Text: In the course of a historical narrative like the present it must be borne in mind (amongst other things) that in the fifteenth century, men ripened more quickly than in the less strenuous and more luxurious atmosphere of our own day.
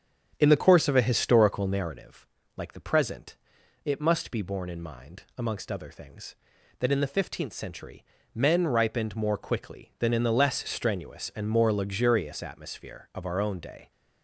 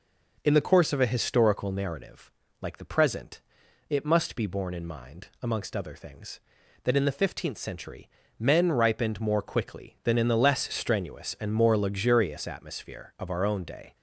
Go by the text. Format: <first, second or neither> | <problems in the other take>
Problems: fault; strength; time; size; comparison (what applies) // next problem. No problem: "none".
second | starts louder than the rest; strong; until 2.0 s; 8.5 dB // pauses between "narrative" and "like"; slight; at 2.2 s; 0.30 s long; slight in the second // pauses between "present" and "it"; noticeable; at 3.3 s; 0.48 s long; noticeable in the second